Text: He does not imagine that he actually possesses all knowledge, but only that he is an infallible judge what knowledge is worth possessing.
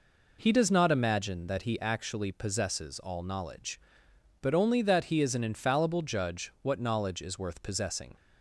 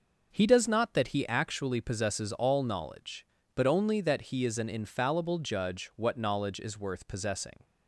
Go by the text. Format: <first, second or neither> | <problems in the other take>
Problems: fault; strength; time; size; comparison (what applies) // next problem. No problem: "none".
first | skips "imagine"; at 0.9 s